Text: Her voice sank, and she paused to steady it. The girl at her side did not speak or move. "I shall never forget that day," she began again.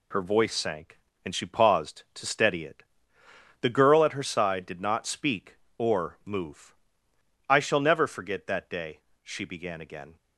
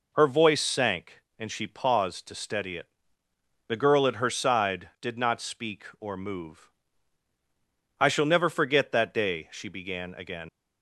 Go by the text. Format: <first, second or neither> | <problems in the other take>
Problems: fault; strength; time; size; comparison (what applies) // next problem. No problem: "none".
first | leaves "again" unfinished; at 10.4 s; 90 ms